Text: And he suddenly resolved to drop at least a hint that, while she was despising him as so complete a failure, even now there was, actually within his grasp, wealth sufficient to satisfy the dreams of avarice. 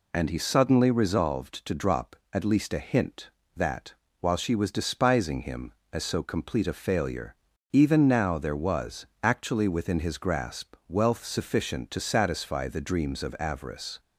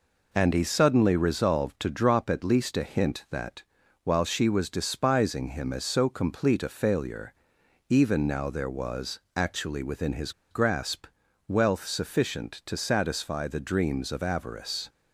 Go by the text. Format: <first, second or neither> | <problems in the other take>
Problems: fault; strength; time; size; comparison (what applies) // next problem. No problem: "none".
first | pauses between "his" and "grasp"; slight; at 10.3 s; 0.19 s long